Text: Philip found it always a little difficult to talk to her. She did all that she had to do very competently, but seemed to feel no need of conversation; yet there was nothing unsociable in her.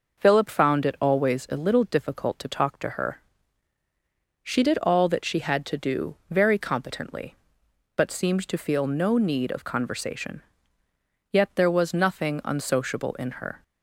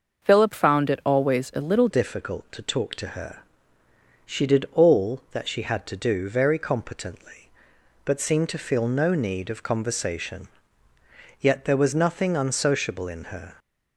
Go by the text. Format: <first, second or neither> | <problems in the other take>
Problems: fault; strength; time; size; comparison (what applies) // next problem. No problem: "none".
first | starts louder than the rest; noticeable; until 1.2 s; 6 dB // changes voice at "difficult"; from 1.8 s on; 11.7 s long